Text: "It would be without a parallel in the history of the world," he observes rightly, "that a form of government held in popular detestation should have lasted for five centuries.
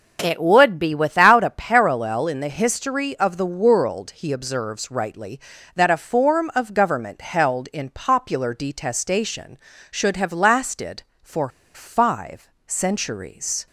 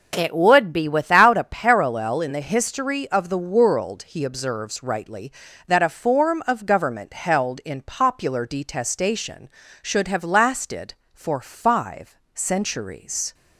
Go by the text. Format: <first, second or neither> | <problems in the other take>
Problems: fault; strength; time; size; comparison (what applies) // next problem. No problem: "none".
second | pauses between "for" and "five"; slight; at 11.4 s; 0.26 s long // pauses between "five" and "centuries"; slight; at 12.4 s; 0.16 s long; slight in the second